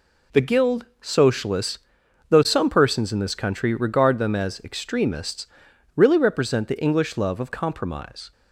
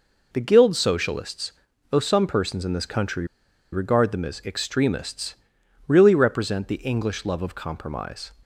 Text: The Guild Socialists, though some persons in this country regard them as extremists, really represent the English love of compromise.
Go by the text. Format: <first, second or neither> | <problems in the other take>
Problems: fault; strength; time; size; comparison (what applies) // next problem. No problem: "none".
first | pauses between "country" and "regard"; noticeable; at 3.2 s; 0.47 s long